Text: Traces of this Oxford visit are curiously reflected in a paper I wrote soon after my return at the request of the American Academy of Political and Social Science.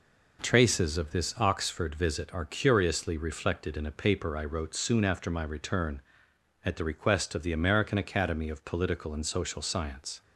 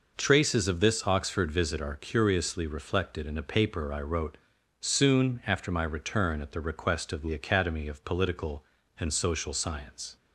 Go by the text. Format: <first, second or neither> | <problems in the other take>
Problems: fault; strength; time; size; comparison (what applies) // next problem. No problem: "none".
first | pauses between "wrote" and "soon"; at 4.3 s; 0.42 s long // skips "American"; at 7.3 s